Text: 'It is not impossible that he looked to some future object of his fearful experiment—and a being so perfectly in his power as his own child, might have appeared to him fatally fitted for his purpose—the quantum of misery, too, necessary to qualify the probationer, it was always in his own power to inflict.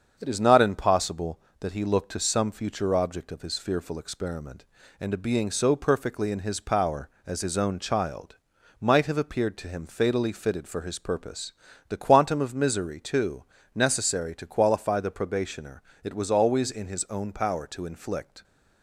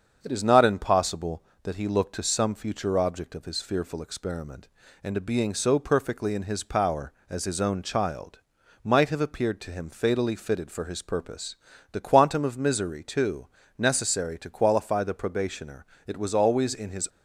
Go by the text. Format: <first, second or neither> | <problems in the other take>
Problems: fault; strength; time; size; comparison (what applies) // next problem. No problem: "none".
first | starts louder than the rest; strong; until 1.2 s; 7 dB; strong in the first // stops before "own power to inflict"; at 17.0 s